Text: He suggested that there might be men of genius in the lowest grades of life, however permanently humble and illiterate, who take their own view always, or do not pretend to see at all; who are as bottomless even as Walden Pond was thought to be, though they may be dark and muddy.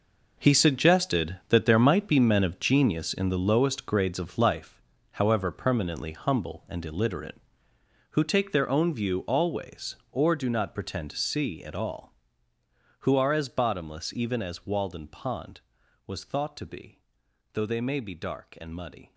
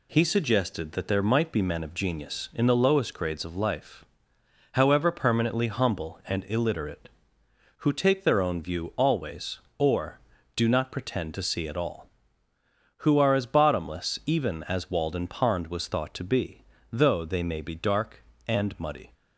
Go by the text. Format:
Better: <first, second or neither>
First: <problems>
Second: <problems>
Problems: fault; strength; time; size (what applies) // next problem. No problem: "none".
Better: second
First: gets quieter; strong; throughout; 13 dB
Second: none